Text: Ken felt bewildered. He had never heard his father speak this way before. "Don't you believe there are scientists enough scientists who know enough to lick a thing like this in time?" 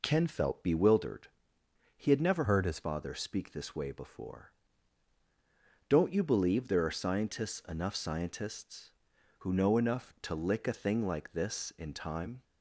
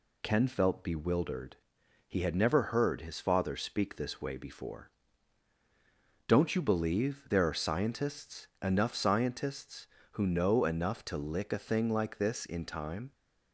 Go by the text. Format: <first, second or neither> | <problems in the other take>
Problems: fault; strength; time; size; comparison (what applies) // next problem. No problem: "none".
second | changes voice from "heard" to "his"; from 2.4 to 2.7 s; 0.3 s long